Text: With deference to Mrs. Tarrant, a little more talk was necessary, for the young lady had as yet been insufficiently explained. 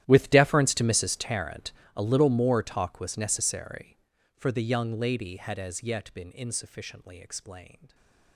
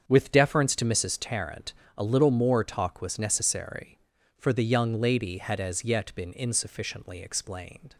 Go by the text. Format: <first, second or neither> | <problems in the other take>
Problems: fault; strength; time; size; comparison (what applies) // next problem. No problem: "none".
second | gets quieter; strong; throughout; 20.5 dB // starts louder than the rest; strong; until 1.0 s; 12.5 dB; strong in the second // stays silent after the last word; slight; from 7.8 s on; 0.5 s long